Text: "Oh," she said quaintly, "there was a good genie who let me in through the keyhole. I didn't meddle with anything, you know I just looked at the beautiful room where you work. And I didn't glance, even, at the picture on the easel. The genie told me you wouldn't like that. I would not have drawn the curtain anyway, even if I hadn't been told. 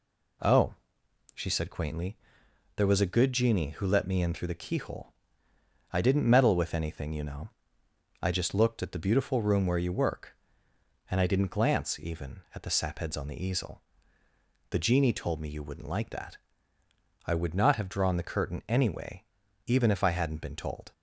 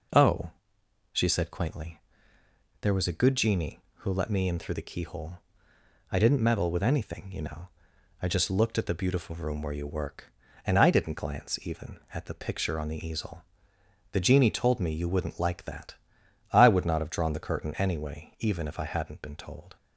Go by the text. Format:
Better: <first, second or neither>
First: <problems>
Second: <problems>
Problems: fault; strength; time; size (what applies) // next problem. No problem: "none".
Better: second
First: pauses between "know" and "I"; noticeable; at 7.5 s; 0.72 s long // says "sapheads" for "picture"; at 12.7 s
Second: pauses between "know" and "I"; noticeable; at 7.6 s; 0.54 s long